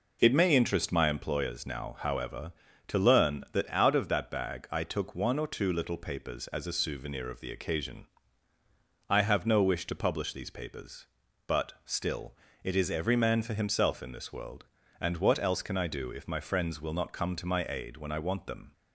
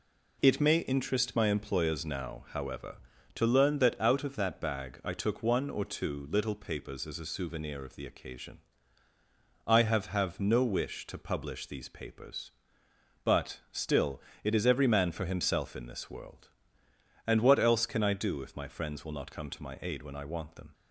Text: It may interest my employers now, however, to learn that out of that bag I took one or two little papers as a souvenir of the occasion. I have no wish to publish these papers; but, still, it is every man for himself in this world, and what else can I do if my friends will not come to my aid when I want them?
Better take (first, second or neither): first